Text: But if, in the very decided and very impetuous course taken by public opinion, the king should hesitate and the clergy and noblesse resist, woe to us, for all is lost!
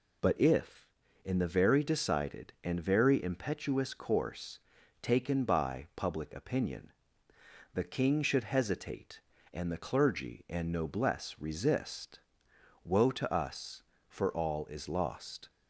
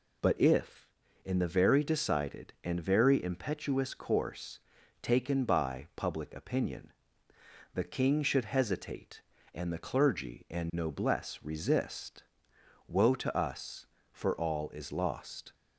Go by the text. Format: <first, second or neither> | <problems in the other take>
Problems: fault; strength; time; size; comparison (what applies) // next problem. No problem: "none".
neither | pauses between "course" and "taken"; the same in both